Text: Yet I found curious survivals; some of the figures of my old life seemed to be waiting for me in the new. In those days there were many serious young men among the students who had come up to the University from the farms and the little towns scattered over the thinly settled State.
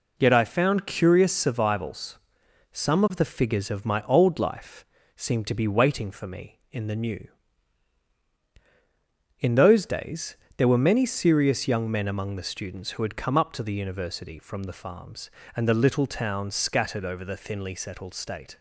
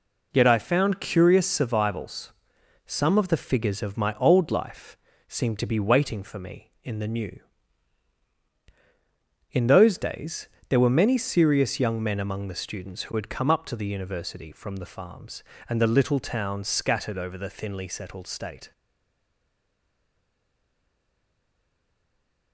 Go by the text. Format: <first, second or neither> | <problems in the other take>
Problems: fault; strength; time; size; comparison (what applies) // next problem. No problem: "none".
first | pauses between "life" and "seemed"; slight; at 4.9 s; 0.30 s long; slight in the first // pauses between "days" and "there"; slight; at 10.4 s; 0.22 s long; slight in the first // stays silent after the last word; strong; from 18.7 s on; 3.8 s long